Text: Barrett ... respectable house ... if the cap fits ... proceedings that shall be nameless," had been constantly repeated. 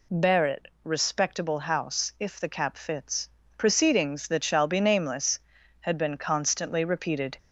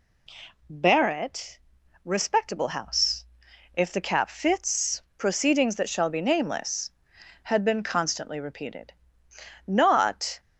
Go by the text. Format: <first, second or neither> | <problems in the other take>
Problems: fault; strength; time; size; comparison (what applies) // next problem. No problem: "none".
first | goes on to say "Not"; noticeable; from 9.6 s on; 0.72 s long